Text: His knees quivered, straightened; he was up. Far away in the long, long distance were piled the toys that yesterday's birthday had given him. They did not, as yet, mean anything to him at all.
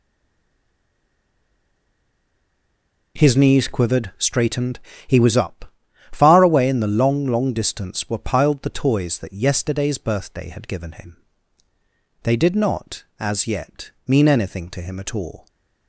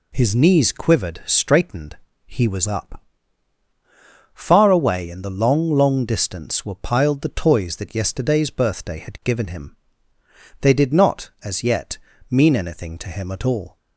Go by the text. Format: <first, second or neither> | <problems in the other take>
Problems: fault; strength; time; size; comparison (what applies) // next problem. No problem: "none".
second | stays silent before the first word; strong; until 3.1 s; 3.1 s long